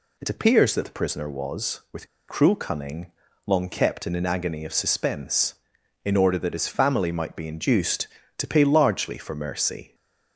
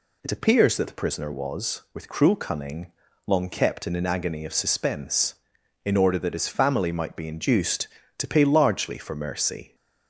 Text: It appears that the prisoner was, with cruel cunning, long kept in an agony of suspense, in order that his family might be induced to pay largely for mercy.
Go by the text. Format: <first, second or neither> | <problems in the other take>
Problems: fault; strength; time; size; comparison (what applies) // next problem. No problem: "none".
second | pauses between "with" and "cruel"; slight; at 2.0 s; 0.21 s long